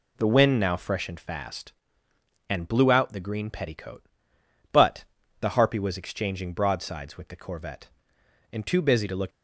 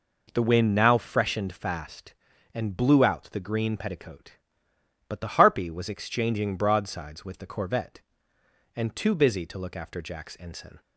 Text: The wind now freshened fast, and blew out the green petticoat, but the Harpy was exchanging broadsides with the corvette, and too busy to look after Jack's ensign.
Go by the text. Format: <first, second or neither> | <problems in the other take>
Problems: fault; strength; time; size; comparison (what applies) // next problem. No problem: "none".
second | pauses between "but" and "the"; at 5.0 s; 0.38 s long // stops before "after Jack's ensign"; at 9.3 s